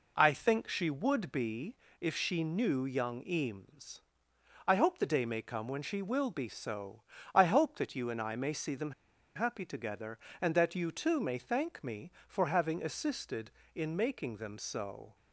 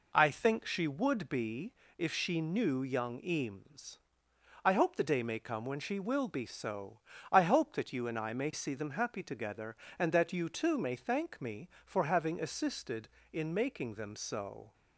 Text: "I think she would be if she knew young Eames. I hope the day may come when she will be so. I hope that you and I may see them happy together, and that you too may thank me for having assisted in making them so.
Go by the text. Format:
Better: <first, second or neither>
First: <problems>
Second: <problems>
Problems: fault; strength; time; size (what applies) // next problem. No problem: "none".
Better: second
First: pauses between "be" and "if"; slight; at 1.7 s; 0.24 s long // pauses between "them" and "happy"; at 8.9 s; 0.44 s long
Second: pauses between "be" and "if"; slight; at 1.7 s; 0.24 s long